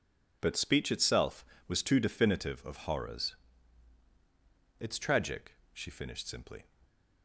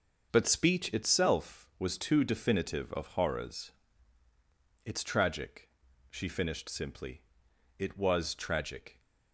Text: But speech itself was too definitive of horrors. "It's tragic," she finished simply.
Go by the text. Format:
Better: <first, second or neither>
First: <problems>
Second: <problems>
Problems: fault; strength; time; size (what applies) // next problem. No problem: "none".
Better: first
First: none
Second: starts louder than the rest; until 1.3 s; 6.5 dB // goes on to say "It was tragic"; noticeable; from 7.7 s on; 1.2 s long